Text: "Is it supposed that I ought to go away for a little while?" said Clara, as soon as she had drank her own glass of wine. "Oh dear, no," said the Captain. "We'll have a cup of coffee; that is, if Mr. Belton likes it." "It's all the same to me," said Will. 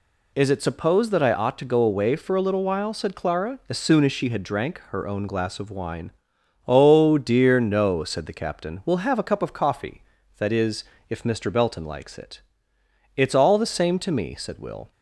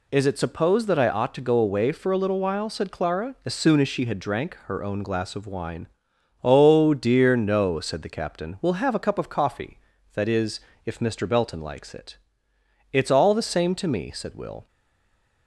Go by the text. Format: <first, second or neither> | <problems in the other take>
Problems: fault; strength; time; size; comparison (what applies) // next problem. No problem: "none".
first | stays silent after the last word; slight; from 14.6 s on; 0.8 s long